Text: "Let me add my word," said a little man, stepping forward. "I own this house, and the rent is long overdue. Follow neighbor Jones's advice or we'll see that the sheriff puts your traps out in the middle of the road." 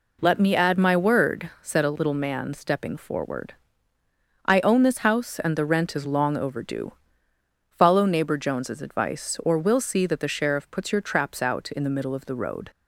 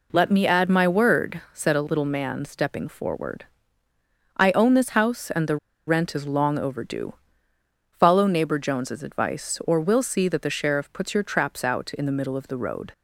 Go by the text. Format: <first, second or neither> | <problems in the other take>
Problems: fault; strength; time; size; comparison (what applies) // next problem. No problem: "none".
first | pauses between "the" and "rent"; slight; at 5.5 s; 0.31 s long